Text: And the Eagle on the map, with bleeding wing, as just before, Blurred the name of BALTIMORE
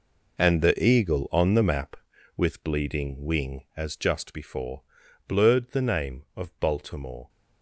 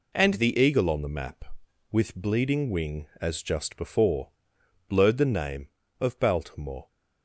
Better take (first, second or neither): second